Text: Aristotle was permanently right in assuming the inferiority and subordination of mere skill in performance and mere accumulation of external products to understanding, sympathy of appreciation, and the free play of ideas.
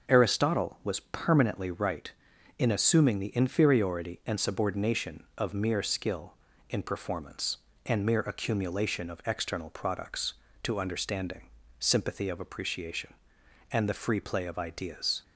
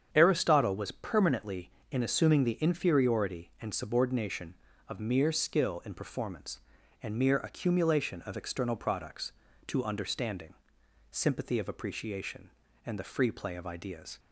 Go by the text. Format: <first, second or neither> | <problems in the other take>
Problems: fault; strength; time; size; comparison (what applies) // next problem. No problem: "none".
first | starts louder than the rest; strong; until 1.1 s; 8 dB // skips "right"; at 1.7 s